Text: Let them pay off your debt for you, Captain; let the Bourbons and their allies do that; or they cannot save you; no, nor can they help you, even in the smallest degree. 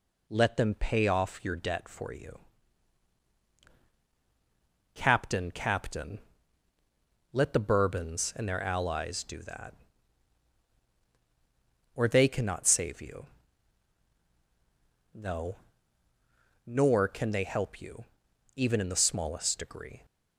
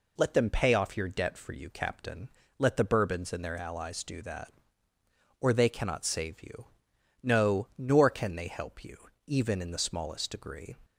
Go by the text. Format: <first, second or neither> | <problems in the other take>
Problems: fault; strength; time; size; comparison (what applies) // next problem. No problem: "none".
second | says "Captain" twice; at 5.5 s